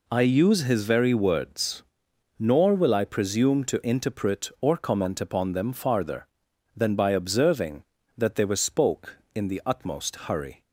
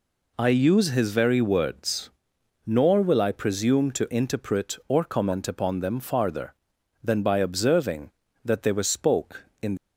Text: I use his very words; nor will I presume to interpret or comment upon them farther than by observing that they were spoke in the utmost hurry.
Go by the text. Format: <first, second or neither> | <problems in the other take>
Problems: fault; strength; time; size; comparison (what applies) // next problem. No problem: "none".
first | stops before "the utmost hurry"; at 9.7 s